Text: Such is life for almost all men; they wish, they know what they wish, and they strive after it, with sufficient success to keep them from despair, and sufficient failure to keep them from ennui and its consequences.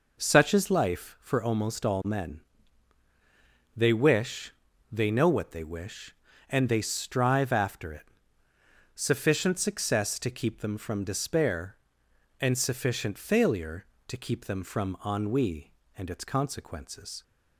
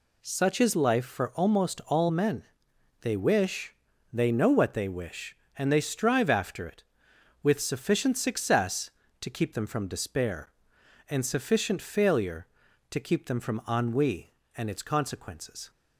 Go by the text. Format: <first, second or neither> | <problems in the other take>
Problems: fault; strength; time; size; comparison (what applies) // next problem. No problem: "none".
second | skips "with"; at 8.4 s